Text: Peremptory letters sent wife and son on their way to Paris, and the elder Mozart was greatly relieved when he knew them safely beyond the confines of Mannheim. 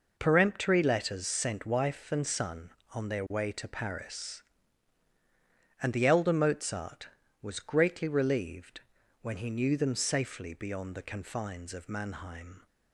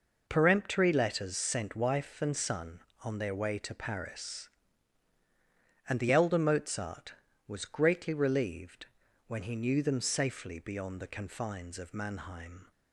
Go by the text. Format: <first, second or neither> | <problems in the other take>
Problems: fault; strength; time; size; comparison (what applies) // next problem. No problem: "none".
neither | pauses between "relieved" and "when"; the same in both